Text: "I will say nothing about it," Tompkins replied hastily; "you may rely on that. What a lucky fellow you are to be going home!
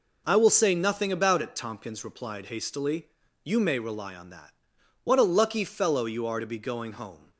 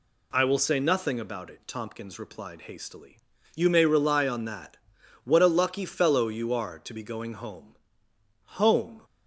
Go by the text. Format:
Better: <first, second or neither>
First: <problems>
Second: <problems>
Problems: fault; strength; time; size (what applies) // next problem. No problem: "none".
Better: first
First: none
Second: says "home" twice; at 8.4 s